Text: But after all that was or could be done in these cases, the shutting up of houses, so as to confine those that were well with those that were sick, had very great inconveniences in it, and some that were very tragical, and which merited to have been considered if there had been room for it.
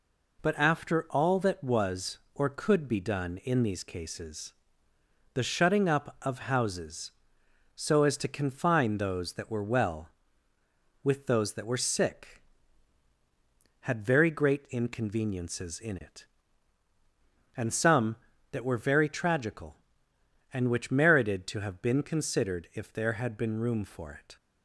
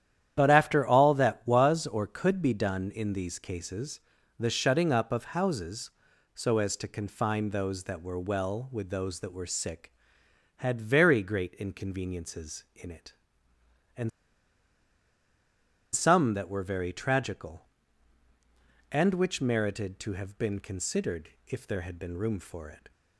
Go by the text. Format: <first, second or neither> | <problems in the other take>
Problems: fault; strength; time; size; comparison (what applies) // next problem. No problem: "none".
first | starts louder than the rest; strong; until 1.3 s; 10.5 dB // pauses between "and" and "some"; strong; at 14.1 s; 1.8 s long // pauses between "considered" and "if"; slight; at 21.3 s; 0.16 s long